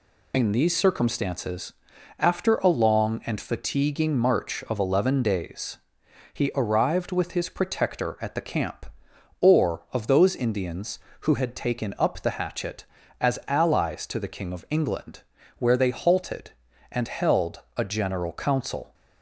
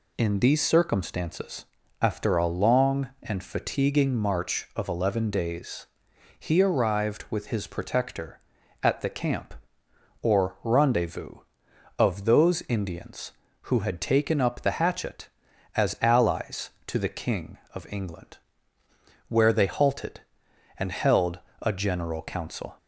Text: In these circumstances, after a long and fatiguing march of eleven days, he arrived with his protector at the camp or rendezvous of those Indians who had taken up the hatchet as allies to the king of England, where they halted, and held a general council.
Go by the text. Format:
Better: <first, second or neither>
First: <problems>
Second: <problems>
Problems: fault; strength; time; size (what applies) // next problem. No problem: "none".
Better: second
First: skips "rendezvous"; at 9.8 s // pauses between "held" and "a"; slight; at 17.6 s; 0.16 s long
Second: pauses between "held" and "a"; slight; at 21.3 s; 0.22 s long